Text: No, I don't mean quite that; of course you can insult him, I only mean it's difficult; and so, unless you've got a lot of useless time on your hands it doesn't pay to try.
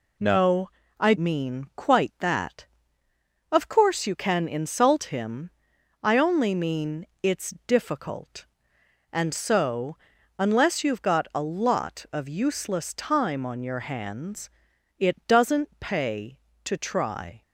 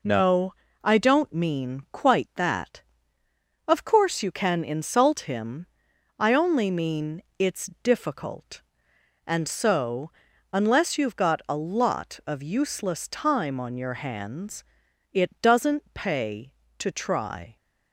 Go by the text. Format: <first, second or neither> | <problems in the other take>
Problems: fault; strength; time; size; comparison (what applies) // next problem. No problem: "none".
second | skips "don't"; at 1.1 s // pauses between "mean" and "it's"; slight; at 7.0 s; 0.16 s long; slight in the second // pauses between "it's" and "difficult"; slight; at 7.5 s; 0.16 s long; slight in the second // pauses between "hands" and "it"; noticeable; at 14.4 s; 0.50 s long; noticeable in the second